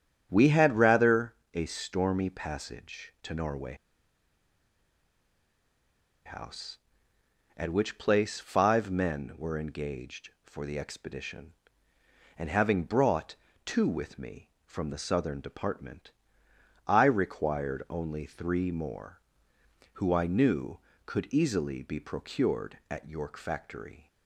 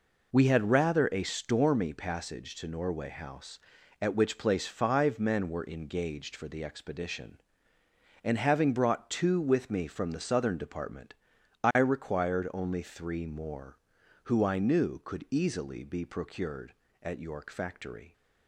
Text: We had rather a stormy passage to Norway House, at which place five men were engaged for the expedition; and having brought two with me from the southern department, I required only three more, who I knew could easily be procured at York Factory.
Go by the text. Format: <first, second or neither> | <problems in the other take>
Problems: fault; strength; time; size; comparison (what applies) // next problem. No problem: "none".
second | starts louder than the rest; strong; until 1.3 s; 8.5 dB // pauses between "rather" and "a"; slight; at 1.3 s; 0.22 s long // pauses between "Norway" and "House"; strong; at 3.7 s; 2.5 s long // pauses between "brought" and "two"; slight; at 13.3 s; 0.30 s long